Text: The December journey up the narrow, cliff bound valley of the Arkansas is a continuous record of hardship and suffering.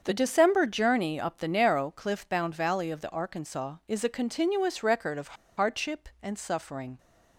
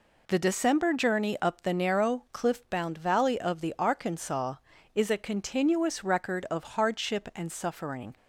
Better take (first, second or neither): second